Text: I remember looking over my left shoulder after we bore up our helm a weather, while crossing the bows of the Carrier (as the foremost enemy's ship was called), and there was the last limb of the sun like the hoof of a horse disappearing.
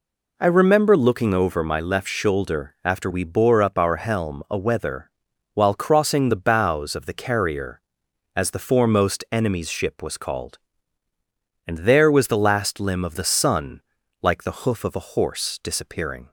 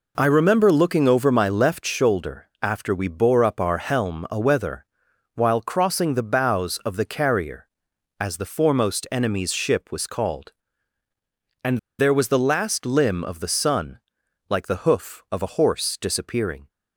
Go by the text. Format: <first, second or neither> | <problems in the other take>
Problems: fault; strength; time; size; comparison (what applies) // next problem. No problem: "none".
first | pauses between "and" and "there"; slight; at 11.7 s; 0.19 s long // pauses between "sun" and "like"; noticeable; at 13.9 s; 0.50 s long; also in the first